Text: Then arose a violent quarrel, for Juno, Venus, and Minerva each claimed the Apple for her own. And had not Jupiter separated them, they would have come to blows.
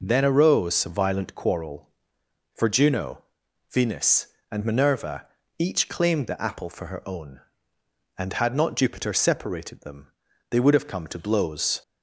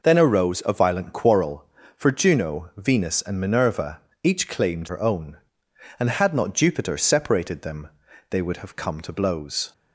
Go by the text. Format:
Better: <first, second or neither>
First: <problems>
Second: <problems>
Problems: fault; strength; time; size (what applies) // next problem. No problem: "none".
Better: first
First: pauses between "Minerva" and "each"; slight; at 5.2 s; 0.32 s long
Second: pauses between "Minerva" and "each"; slight; at 3.9 s; 0.22 s long // skips "the Apple for"; at 4.8 s